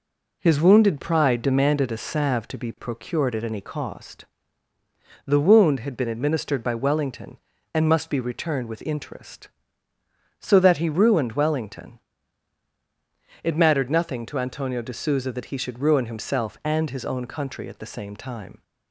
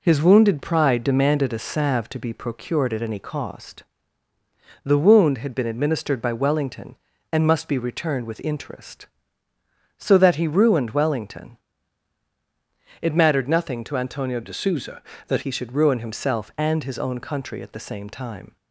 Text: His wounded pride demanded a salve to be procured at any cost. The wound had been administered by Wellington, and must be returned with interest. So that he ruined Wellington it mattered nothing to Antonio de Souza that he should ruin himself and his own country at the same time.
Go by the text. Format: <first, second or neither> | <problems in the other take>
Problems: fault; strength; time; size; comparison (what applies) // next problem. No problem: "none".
first | pauses between "Wellington" and "it"; strong; at 11.5 s; 1.4 s long; strong in the first // changes voice from "de" to "that"; from 14.4 to 15.4 s; 1.0 s long